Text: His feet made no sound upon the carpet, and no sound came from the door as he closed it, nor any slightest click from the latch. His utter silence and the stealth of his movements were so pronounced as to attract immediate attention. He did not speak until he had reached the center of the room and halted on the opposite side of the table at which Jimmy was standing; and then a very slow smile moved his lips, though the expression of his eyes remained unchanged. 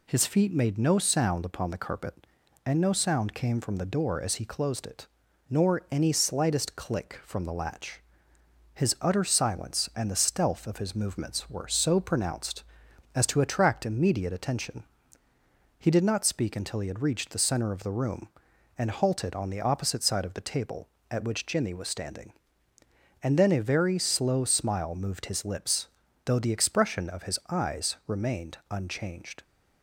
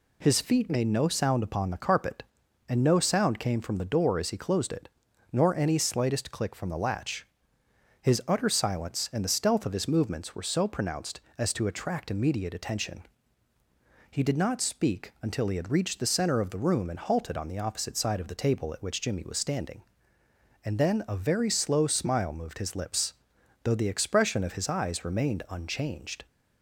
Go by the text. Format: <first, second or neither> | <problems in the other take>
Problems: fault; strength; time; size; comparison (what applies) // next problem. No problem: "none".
neither | none